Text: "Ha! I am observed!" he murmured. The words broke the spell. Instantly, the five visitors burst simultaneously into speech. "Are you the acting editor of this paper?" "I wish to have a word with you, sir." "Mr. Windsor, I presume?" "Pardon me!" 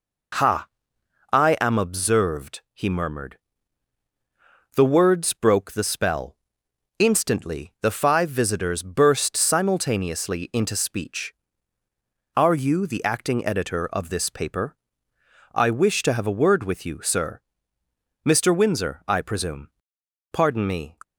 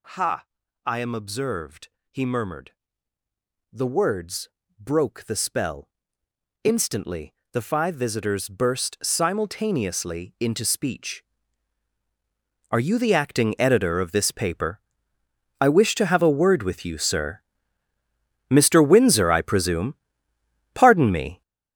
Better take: first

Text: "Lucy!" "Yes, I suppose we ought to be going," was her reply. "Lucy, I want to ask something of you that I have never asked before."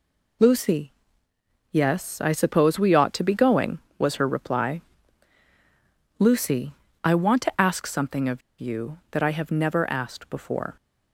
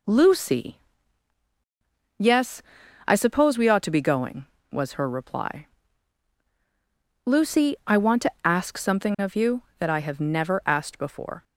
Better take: second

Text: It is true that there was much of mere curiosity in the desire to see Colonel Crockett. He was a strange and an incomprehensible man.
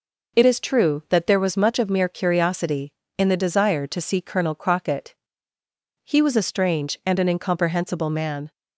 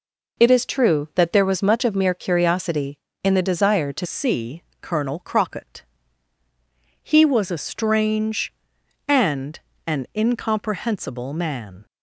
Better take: first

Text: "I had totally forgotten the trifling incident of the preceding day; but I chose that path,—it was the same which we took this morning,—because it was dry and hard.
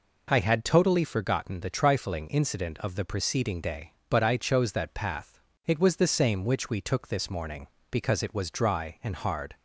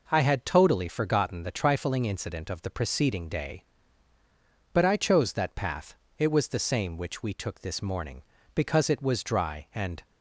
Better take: first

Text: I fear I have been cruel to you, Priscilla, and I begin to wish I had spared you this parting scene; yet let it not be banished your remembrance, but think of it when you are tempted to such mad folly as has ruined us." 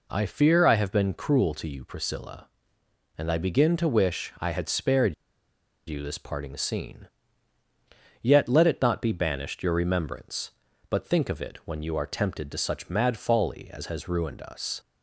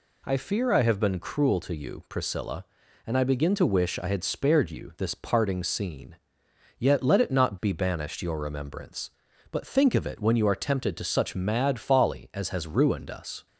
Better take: second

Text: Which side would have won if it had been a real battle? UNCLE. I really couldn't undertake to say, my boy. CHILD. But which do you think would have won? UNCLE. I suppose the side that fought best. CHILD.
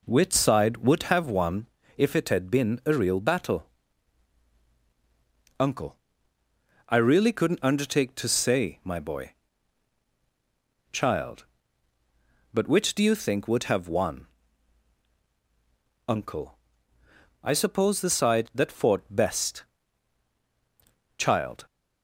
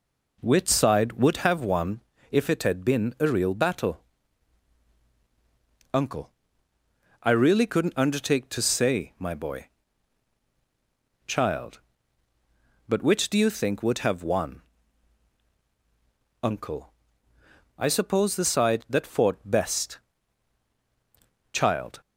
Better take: neither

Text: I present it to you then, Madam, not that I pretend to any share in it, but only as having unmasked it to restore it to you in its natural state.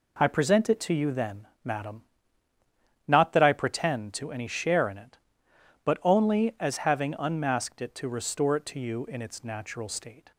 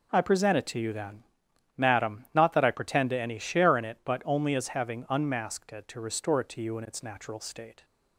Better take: neither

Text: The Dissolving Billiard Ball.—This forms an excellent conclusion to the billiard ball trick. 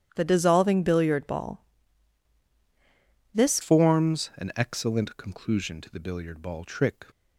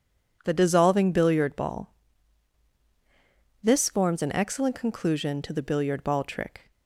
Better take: second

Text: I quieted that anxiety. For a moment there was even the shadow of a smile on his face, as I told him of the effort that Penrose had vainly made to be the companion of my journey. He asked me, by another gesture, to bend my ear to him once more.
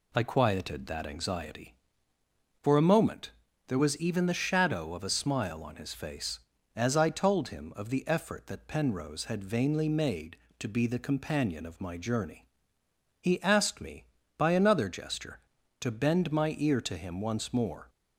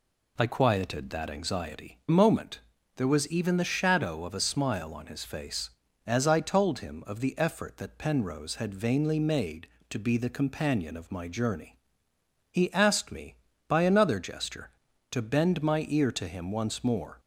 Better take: first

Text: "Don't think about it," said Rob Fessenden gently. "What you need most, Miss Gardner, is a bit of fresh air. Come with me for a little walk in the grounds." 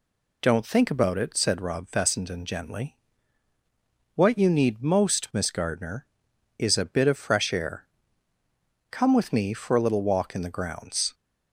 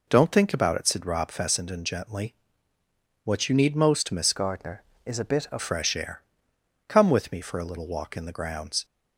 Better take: first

